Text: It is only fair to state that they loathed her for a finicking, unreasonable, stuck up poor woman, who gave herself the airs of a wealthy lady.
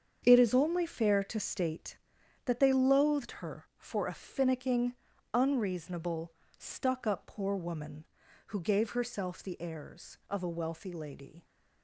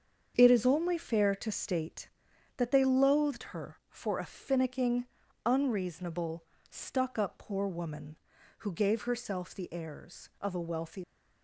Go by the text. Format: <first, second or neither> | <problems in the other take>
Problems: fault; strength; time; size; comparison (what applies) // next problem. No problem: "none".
first | starts louder than the rest; strong; until 1.3 s; 7.5 dB; strong in the first // stops before "lady"; at 11.0 s